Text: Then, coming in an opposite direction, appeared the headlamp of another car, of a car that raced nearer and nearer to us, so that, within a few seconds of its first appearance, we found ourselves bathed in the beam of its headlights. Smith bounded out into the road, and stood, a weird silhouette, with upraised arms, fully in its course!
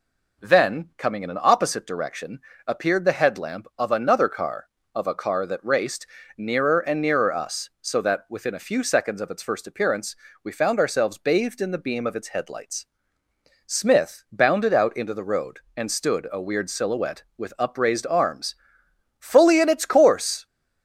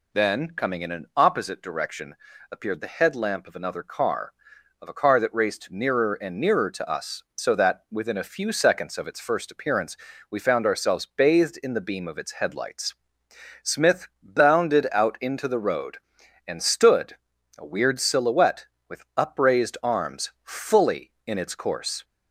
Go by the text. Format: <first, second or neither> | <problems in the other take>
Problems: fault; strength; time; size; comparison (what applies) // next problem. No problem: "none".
second | pauses between "raced" and "nearer"; slight; at 6.0 s; 0.30 s long // skips "to"; at 7.3 s